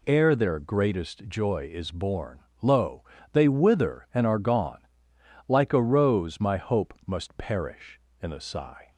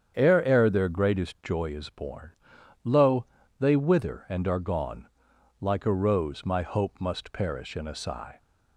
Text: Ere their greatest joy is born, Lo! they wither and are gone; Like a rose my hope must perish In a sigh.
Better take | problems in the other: first | starts louder than the rest; strong; until 1.1 s; 8 dB // says "Ere" twice; at 0.4 s

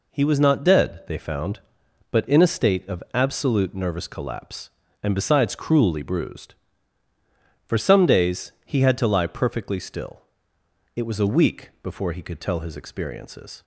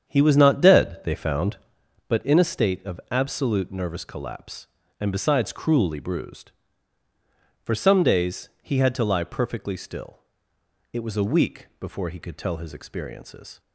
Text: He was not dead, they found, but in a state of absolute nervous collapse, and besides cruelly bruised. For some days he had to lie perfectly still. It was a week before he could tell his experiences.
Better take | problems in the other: first | starts louder than the rest; strong; until 1.8 s; 8 dB

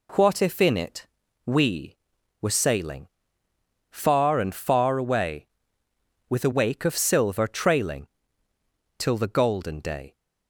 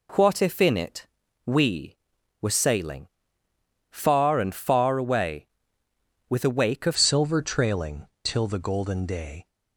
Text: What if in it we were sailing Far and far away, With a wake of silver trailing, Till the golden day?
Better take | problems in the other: first | pauses between "it" and "we"; at 1.0 s; 0.40 s long; also in the first // pauses between "sailing" and "Far"; noticeable; at 3.0 s; 0.86 s long; noticeable in the first // changes voice at "silver"; from 6.9 s on; 2.5 s long

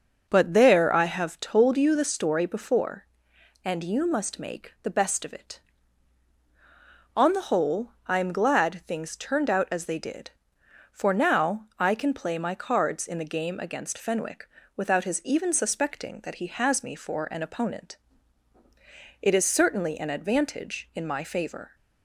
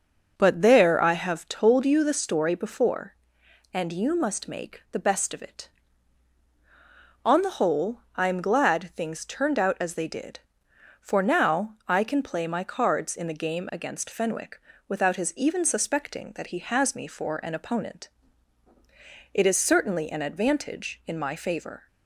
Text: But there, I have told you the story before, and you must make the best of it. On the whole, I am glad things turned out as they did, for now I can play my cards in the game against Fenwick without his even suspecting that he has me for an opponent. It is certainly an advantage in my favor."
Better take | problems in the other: neither | starts louder than the rest; noticeable; the same in both // pauses between "Fenwick" and "without"; slight; the same in both

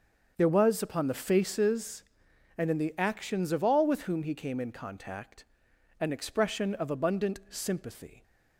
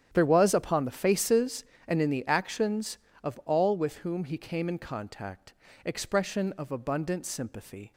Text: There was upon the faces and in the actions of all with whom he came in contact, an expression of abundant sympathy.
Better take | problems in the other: first | starts louder than the rest; strong; until 1.1 s; 9.5 dB; also in the first // skips "an"; at 5.6 s

